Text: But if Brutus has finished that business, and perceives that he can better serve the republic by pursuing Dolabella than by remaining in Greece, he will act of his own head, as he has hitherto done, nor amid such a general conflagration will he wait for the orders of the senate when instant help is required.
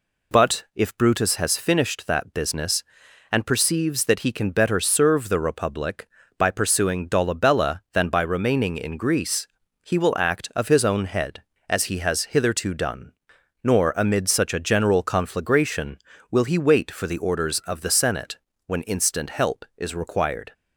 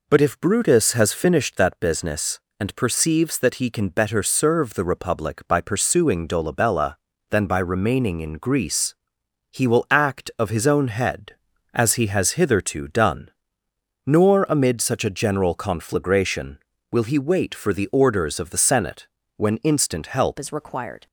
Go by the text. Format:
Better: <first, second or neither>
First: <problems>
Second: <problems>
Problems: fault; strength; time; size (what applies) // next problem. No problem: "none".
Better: first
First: pauses between "senate" and "when"; slight; at 18.3 s; 0.30 s long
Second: pauses between "senate" and "when"; slight; at 19.0 s; 0.26 s long // changes voice at "is"; from 20.3 s on; 0.7 s long